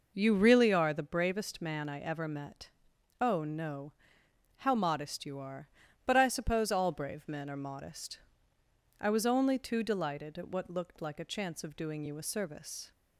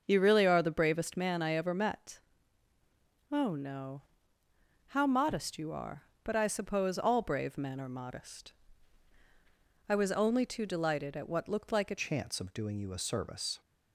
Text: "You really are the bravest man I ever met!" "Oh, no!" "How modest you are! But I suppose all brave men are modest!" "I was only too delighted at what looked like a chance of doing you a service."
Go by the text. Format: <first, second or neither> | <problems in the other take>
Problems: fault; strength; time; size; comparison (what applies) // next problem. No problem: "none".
first | starts louder than the rest; until 1.0 s; 6.5 dB // changes voice at "chance"; from 11.9 s on; 1.7 s long